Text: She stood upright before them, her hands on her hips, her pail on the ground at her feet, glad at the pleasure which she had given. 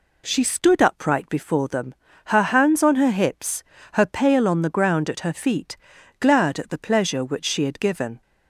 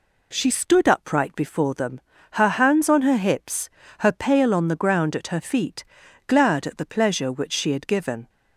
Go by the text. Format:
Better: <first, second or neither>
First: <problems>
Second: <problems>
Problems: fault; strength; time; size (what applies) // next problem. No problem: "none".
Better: neither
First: none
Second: none